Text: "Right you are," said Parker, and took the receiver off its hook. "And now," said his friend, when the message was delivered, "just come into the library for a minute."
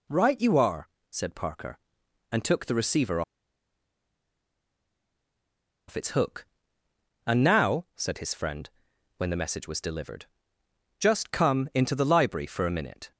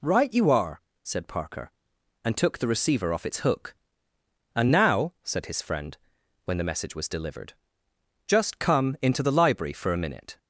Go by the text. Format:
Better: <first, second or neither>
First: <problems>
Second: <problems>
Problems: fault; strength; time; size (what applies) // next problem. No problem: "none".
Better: second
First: pauses between "receiver" and "off"; strong; at 3.2 s; 2.6 s long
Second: none